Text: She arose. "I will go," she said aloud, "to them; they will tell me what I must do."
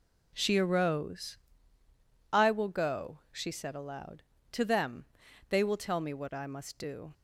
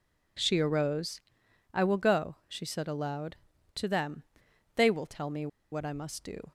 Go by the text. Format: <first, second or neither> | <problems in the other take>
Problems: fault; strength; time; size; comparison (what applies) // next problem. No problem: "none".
first | pauses between "me" and "what"; slight; at 5.4 s; 0.24 s long